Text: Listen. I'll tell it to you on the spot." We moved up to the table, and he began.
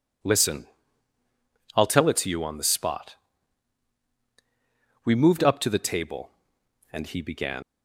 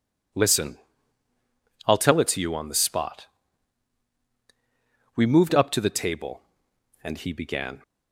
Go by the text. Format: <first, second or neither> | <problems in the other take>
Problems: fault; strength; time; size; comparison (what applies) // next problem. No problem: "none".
second | leaves "began" unfinished; at 7.6 s; 85 ms